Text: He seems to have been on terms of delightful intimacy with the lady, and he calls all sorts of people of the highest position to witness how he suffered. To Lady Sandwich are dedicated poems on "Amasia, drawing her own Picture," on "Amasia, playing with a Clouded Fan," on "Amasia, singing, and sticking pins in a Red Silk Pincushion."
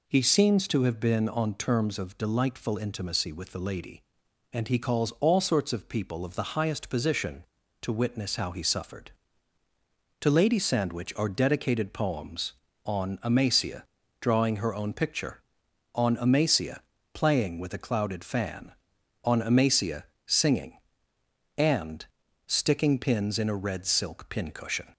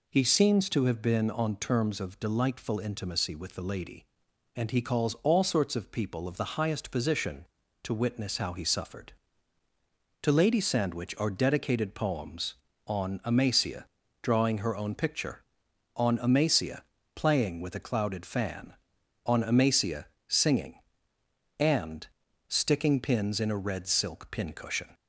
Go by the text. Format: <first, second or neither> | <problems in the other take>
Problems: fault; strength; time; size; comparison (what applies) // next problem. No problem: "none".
neither | pauses between "and" and "sticking"; the same in both